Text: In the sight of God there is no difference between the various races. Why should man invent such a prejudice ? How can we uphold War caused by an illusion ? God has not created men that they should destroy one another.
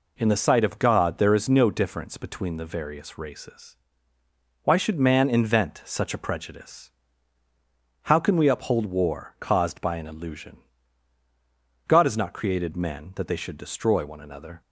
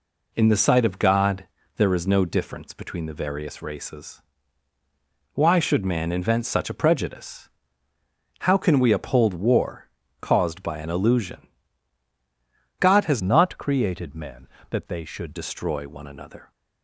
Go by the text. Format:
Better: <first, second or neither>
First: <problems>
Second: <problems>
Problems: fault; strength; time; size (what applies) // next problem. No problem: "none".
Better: first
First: none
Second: pauses between "God" and "there"; slight; at 1.4 s; 0.30 s long // pauses between "War" and "caused"; slight; at 9.9 s; 0.32 s long // changes voice from "not" to "should"; from 13.2 to 15.3 s; 2.1 s long